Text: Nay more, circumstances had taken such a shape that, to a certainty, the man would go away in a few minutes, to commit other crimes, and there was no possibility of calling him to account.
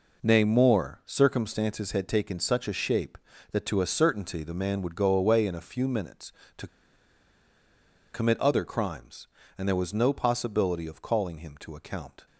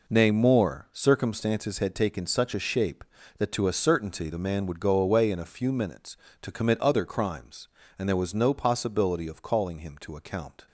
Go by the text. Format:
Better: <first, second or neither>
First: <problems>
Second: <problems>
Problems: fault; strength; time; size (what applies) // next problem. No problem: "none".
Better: second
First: pauses between "to" and "commit"; strong; at 6.6 s; 1.4 s long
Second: none